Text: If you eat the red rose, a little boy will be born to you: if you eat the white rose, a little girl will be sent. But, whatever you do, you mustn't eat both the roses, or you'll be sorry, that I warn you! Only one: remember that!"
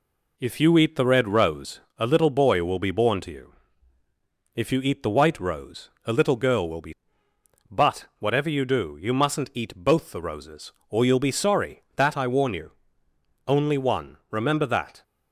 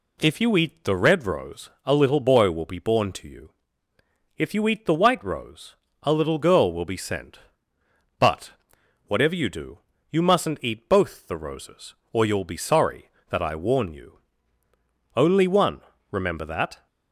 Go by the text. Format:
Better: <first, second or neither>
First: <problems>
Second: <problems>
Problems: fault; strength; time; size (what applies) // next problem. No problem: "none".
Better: second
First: skips "sent"; at 7.3 s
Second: none